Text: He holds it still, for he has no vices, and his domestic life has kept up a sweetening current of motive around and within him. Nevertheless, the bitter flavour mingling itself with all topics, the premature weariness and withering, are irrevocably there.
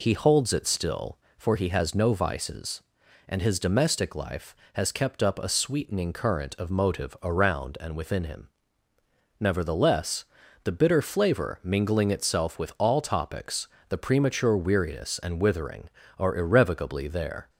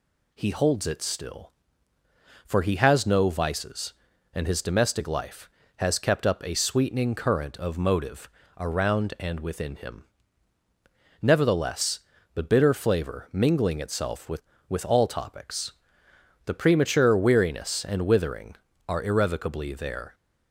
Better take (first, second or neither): first